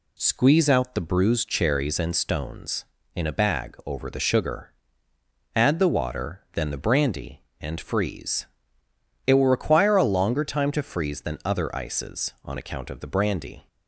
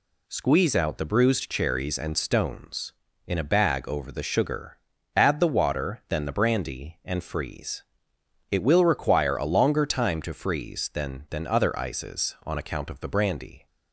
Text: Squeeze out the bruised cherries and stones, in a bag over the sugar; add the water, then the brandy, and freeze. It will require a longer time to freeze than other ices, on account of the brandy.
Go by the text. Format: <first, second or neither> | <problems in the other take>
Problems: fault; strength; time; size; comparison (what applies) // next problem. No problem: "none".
first | says "than" twice; at 11.2 s